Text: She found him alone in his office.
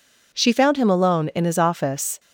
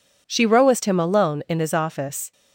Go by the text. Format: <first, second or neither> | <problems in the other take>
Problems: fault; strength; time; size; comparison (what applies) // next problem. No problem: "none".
first | says "rowest" for "found"; at 0.4 s